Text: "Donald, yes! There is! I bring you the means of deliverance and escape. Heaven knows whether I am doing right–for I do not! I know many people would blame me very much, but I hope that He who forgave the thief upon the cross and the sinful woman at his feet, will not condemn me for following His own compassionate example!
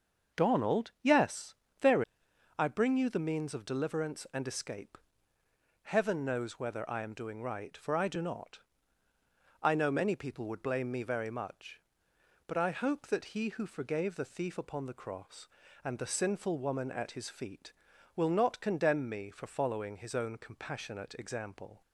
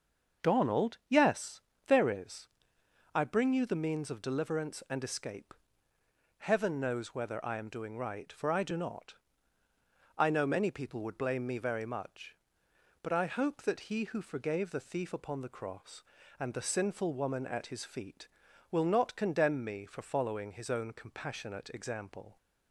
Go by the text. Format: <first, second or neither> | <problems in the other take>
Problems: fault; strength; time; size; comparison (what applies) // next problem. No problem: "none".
second | starts louder than the rest; until 1.4 s; 6.5 dB; also in the second // skips "is"; at 2.2 s